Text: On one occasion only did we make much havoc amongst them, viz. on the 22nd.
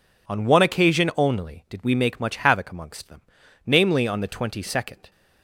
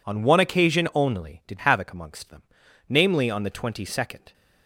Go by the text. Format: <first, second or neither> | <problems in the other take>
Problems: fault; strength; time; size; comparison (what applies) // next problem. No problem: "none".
first | skips "we make much"; at 1.5 s